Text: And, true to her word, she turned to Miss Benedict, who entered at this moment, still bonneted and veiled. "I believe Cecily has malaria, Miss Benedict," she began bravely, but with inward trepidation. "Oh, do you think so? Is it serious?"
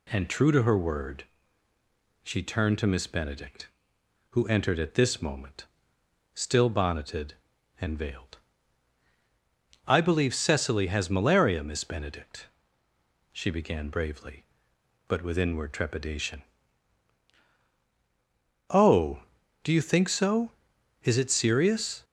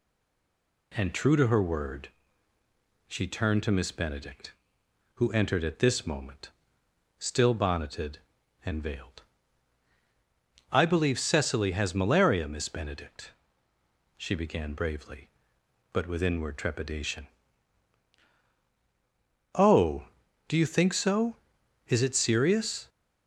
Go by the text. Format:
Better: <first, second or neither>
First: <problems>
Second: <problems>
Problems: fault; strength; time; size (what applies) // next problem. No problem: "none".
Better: first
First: none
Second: stays silent before the first word; slight; until 0.9 s; 0.9 s long